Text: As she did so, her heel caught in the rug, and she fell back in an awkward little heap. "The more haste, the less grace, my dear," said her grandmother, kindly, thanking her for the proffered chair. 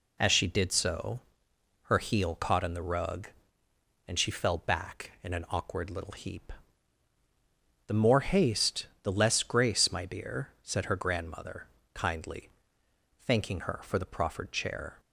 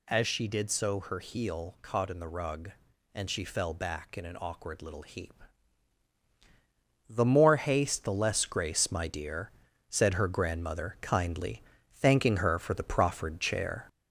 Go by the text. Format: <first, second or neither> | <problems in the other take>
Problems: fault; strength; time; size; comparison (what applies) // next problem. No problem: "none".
first | gets louder; throughout; 3.5 dB